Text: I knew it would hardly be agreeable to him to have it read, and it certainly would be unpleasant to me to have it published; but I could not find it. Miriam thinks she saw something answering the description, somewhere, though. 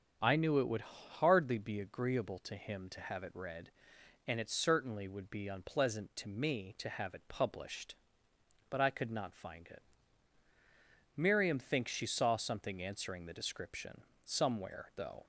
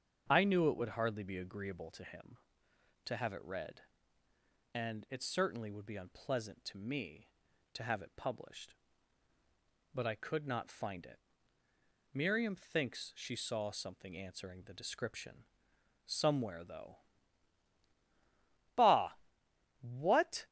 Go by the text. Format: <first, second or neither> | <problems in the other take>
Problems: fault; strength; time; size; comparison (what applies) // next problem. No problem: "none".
first | starts louder than the rest; strong; until 1.3 s; 7.5 dB // goes on to say "Bah What"; strong; from 18.7 s on; 1.7 s long